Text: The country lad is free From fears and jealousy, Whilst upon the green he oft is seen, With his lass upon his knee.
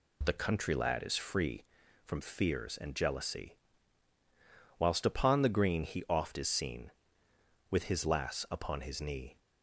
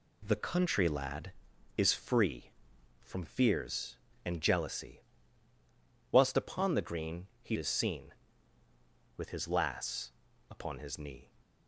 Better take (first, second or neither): first